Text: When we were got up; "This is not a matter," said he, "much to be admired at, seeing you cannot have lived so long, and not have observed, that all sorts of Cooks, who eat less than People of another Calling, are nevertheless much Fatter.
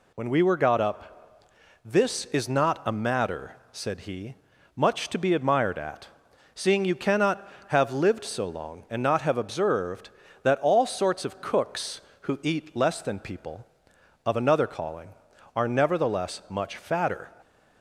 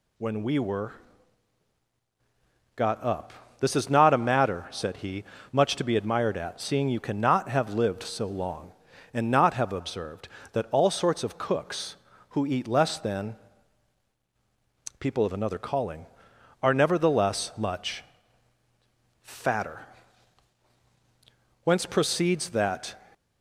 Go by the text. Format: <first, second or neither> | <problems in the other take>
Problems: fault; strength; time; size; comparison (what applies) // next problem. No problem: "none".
first | pauses between "were" and "got"; strong; at 0.9 s; 1.8 s long // pauses between "than" and "People"; strong; at 13.3 s; 1.6 s long // pauses between "much" and "Fatter"; at 18.0 s; 1.1 s long // goes on to say "Whence proceeds that"; from 21.6 s on; 1.3 s long